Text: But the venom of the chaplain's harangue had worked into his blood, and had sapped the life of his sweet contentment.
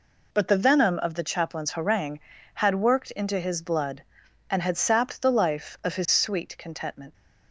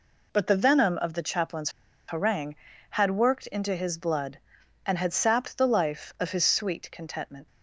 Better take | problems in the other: first | pauses between "chaplain's" and "harangue"; at 1.7 s; 0.36 s long

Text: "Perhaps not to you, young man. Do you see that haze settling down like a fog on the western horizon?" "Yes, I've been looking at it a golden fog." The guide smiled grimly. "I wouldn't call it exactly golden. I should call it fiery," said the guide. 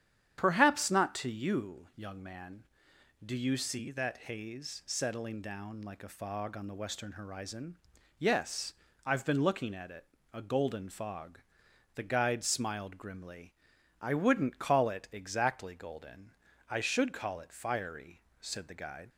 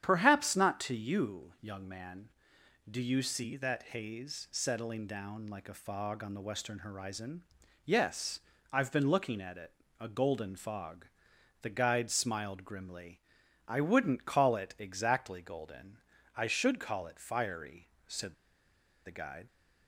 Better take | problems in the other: first | starts louder than the rest; strong; until 1.0 s; 9.5 dB; strong in the first // pauses between "that" and "haze"; slight; at 3.8 s; 0.16 s long; slight in the first // pauses between "it" and "a"; slight; at 9.7 s; 0.26 s long; slight in the first // pauses between "said" and "the"; noticeable; at 18.3 s; 0.71 s long

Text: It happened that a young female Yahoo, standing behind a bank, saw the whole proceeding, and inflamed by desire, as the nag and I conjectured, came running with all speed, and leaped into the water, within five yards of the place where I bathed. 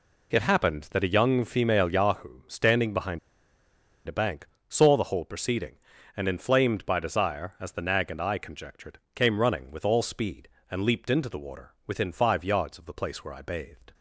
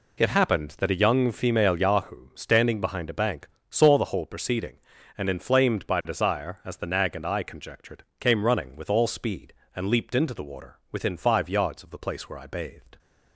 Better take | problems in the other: second | pauses between "behind" and "a"; noticeable; at 3.1 s; 0.88 s long

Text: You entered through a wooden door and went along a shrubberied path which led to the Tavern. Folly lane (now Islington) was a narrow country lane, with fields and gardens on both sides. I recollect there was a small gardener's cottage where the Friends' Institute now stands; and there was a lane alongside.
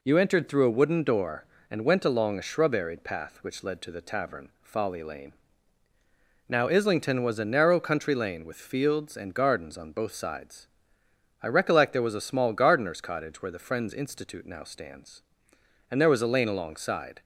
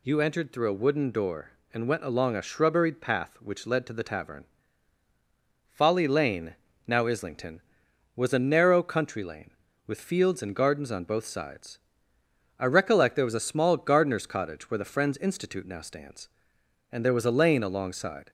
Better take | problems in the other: neither | none

